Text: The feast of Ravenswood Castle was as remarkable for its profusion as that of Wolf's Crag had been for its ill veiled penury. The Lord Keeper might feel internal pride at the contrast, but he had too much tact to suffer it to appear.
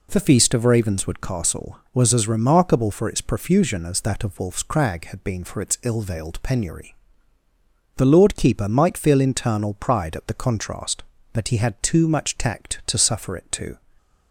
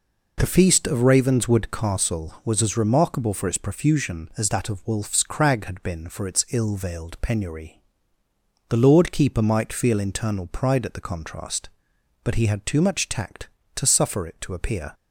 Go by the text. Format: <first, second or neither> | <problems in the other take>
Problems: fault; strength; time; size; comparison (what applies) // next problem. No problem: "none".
second | stops before "appear"; at 13.9 s